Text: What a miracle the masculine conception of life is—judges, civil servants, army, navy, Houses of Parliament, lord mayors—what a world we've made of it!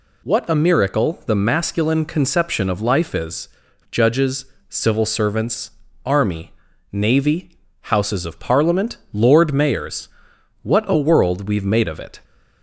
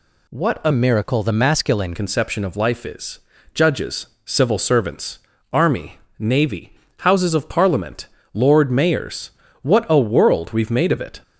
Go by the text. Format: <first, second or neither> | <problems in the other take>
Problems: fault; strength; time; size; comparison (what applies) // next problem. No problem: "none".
first | changes voice from "miracle" to "masculine"; from 0.7 to 1.9 s; 1.2 s long